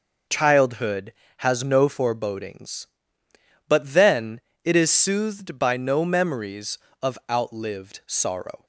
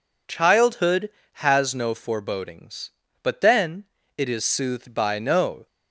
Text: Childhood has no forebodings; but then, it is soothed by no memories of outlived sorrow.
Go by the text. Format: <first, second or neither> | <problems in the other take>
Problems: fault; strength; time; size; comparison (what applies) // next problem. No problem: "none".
first | stops before "memories of outlived sorrow"; at 5.6 s